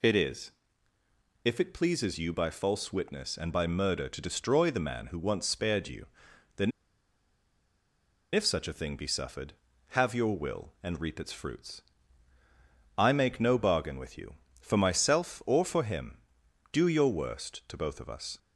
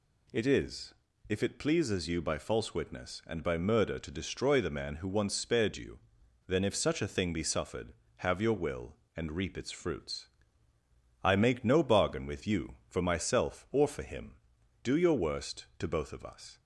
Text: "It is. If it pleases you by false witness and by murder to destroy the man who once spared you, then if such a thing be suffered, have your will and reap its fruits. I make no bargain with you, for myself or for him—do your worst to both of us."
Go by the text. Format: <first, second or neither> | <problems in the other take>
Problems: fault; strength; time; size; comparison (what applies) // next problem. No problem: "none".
second | pauses between "then" and "if"; strong; at 6.7 s; 1.6 s long